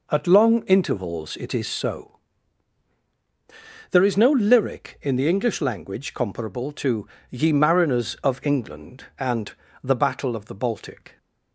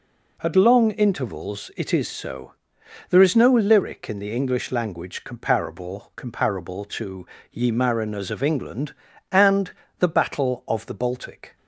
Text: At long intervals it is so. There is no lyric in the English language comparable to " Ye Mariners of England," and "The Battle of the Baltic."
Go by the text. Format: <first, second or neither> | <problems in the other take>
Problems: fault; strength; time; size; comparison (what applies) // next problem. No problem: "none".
first | says "comparable" twice; at 6.1 s // pauses between "and" and "The"; slight; at 9.7 s; 0.26 s long; slight in the first